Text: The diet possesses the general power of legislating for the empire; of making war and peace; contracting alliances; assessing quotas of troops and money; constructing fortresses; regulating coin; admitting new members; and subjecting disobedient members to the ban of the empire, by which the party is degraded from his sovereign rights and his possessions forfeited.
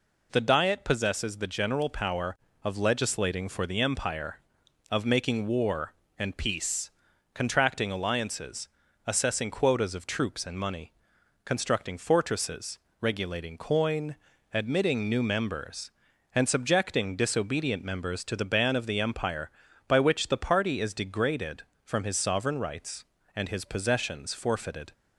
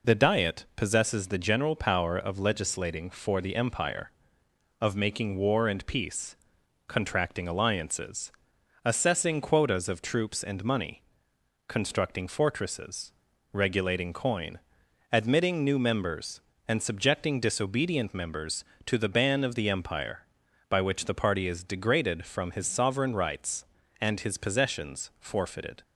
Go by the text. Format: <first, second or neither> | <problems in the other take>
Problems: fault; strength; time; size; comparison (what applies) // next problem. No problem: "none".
neither | none